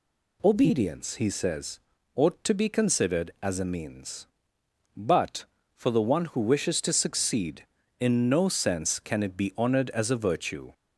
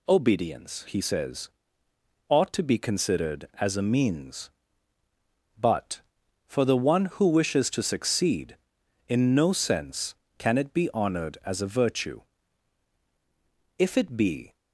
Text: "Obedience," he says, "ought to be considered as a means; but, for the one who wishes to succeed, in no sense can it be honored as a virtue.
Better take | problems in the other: first | goes on to say "If it be"; noticeable; from 13.7 s on; 0.78 s long

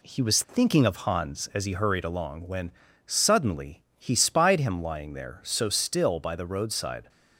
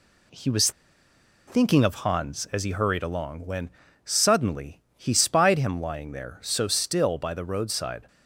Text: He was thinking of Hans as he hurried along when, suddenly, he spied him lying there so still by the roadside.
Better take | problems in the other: first | pauses between "was" and "thinking"; noticeable; at 0.7 s; 0.76 s long

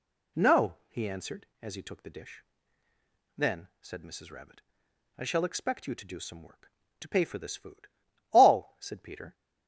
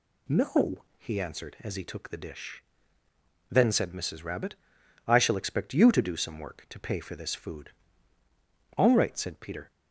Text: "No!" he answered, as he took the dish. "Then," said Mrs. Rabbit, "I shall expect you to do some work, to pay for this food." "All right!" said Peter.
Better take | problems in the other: second | skips "right"; at 8.7 s

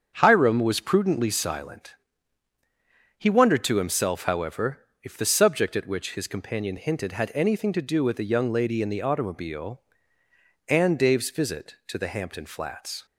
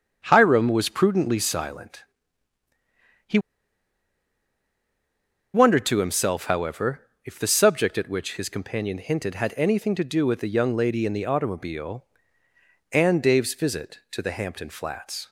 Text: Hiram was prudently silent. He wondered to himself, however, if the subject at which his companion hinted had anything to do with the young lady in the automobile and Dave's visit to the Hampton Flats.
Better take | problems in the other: first | starts louder than the rest; strong; until 1.2 s; 7.5 dB; strong in the first // pauses between "He" and "wondered"; strong; at 3.4 s; 2.1 s long

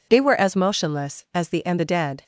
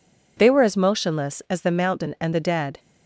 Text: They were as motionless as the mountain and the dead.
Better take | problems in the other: second | skips "mountain"; at 1.6 s

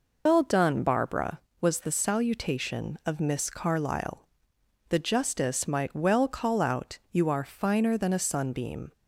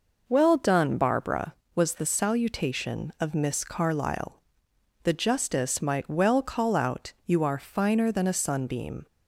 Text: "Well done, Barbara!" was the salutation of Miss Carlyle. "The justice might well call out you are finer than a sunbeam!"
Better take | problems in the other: second | loses the start of "Well"; at 0.2 s; 115 ms

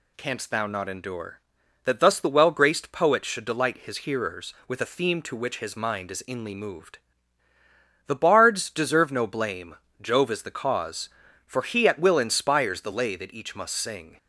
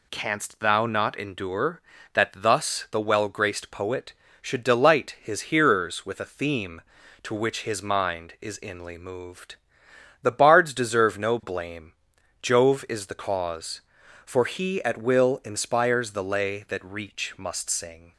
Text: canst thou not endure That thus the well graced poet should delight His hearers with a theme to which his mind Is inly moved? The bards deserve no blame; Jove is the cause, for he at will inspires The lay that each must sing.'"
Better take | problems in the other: first | says "reach" for "each"; at 16.8 s

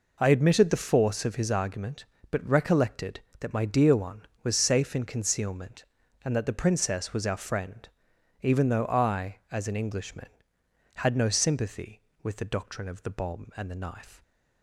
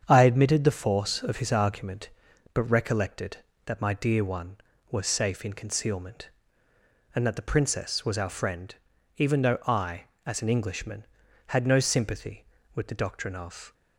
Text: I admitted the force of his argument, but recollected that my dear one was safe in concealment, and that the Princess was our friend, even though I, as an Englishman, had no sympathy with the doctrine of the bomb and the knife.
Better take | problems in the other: first | starts louder than the rest; strong; until 1.0 s; 7.5 dB // stops before "the bomb and the knife"; at 13.7 s

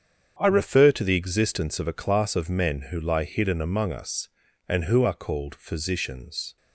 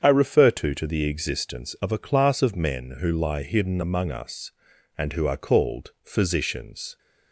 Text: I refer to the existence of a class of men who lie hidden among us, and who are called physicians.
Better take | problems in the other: first | starts louder than the rest; strong; until 1.0 s; 7.5 dB; strong in the first // says "to" twice; at 0.7 s

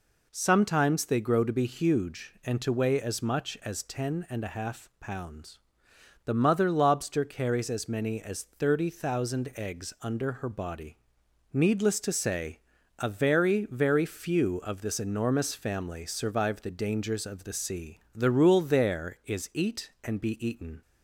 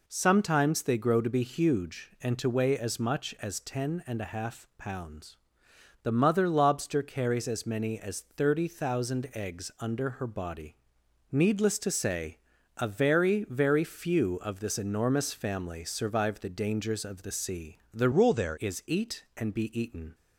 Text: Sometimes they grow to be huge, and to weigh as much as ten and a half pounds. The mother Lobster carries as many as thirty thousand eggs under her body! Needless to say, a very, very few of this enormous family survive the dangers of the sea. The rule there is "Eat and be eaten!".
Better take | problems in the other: first | changes voice from "rule" to "there"; from 18.1 to 18.5 s; 0.4 s long

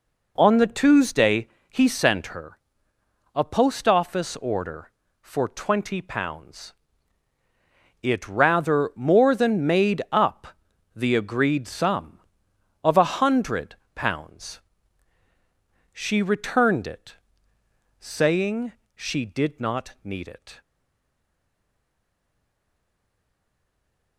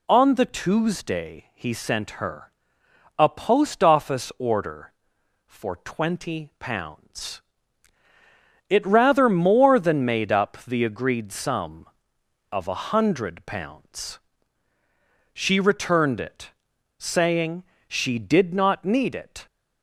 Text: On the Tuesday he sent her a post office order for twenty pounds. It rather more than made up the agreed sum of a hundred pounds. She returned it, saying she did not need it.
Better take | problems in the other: second | pauses between "Tuesday" and "he"; slight; at 1.4 s; 0.18 s long // pauses between "her" and "a"; noticeable; at 2.5 s; 0.76 s long; noticeable in the second // pauses between "up" and "the"; noticeable; at 10.4 s; 0.46 s long // pauses between "hundred" and "pounds"; slight; at 13.7 s; 0.18 s long // pauses between "saying" and "she"; slight; at 18.7 s; 0.22 s long; slight in the second // stays silent after the last word; strong; from 20.6 s on; 3.5 s long

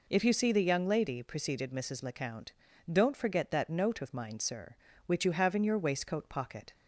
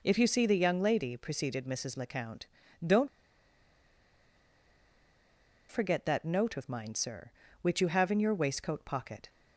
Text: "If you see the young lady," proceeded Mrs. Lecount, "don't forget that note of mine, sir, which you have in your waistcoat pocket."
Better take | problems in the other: first | pauses between "don't" and "forget"; strong; at 3.0 s; 2.6 s long

